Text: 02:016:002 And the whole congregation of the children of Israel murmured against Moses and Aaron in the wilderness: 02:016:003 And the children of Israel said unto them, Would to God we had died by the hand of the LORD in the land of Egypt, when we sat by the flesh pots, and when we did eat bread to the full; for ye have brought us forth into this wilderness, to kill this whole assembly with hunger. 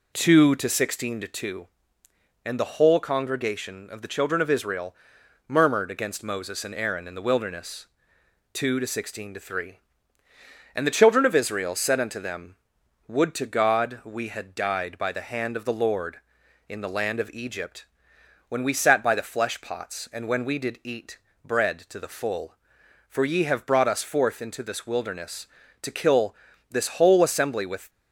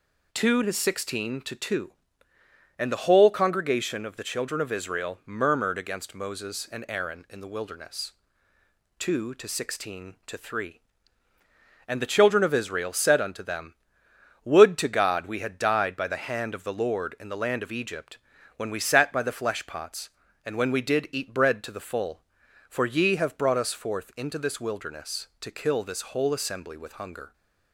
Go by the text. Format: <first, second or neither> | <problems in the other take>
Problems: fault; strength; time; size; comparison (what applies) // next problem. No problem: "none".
second | pauses between "Israel" and "murmured"; noticeable; at 4.9 s; 0.54 s long // pauses between "eat" and "bread"; slight; at 21.1 s; 0.26 s long // pauses between "kill" and "this"; slight; at 26.3 s; 0.36 s long // stops before "hunger"; at 27.8 s